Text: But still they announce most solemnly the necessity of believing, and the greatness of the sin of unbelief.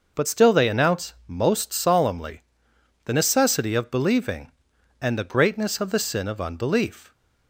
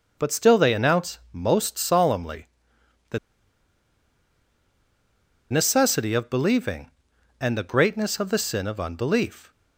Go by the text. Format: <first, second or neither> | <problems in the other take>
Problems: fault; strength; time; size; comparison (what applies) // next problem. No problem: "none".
first | pauses between "solemnly" and "the"; noticeable; at 2.4 s; 0.62 s long; noticeable in the first // pauses between "the" and "necessity"; strong; at 3.1 s; 2.3 s long